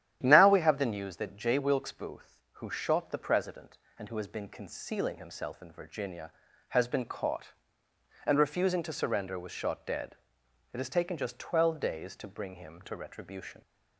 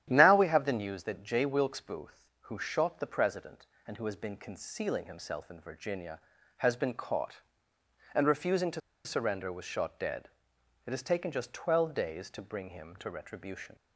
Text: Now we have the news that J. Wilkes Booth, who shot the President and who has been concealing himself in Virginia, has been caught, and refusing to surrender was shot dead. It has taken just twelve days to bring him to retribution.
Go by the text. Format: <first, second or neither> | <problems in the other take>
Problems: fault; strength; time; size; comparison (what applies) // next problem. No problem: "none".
first | starts louder than the rest; strong; until 1.1 s; 11 dB; strong in the first // pauses between "to" and "surrender"; slight; at 8.8 s; 0.25 s long